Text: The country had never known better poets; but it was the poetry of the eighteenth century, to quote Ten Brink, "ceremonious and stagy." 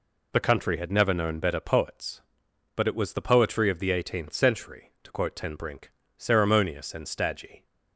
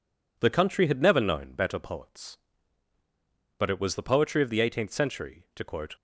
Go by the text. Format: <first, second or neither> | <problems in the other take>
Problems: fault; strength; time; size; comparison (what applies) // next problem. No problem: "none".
first | stops before "Ten Brink ceremonious and stagy"; at 5.9 s